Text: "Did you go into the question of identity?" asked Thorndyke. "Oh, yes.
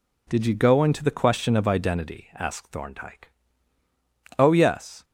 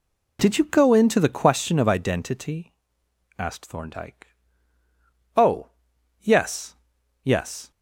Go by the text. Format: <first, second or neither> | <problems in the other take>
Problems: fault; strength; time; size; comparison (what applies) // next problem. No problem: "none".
first | says "yes" twice; at 7.2 s